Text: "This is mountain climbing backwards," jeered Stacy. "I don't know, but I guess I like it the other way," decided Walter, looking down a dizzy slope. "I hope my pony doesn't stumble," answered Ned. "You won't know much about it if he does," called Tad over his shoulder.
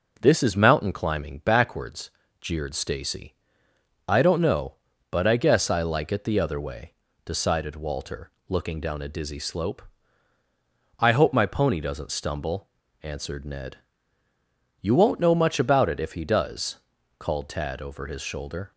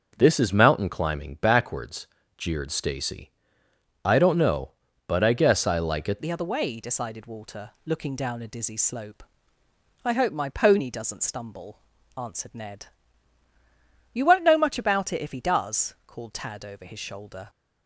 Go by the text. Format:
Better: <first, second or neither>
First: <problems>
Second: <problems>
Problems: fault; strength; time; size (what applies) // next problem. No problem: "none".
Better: first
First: none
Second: starts louder than the rest; until 1.1 s; 6 dB // changes voice at "the"; from 6.2 s on; 11.2 s long